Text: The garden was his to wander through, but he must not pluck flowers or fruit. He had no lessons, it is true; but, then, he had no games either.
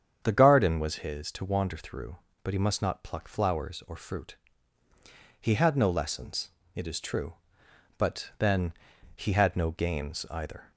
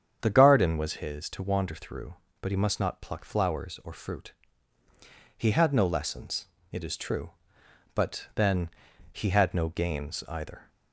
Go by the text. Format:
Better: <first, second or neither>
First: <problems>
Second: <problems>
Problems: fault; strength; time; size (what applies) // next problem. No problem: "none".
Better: neither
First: starts louder than the rest; strong; until 1.2 s; 8 dB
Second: starts louder than the rest; strong; until 1.2 s; 8 dB